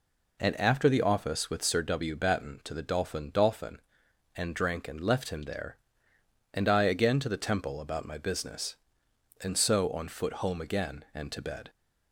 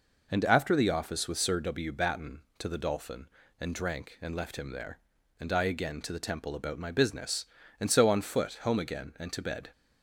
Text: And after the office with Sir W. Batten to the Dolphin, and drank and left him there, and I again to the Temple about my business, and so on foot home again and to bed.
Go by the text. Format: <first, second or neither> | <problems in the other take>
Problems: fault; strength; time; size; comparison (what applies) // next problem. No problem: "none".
second | says "Dolphin" twice; at 3.3 s